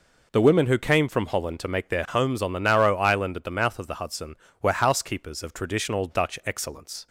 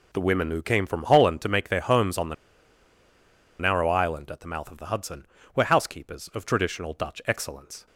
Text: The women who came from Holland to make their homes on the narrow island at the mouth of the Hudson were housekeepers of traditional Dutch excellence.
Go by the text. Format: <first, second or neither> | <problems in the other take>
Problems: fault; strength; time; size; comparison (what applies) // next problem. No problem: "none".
first | pauses between "the" and "narrow"; strong; at 2.3 s; 1.2 s long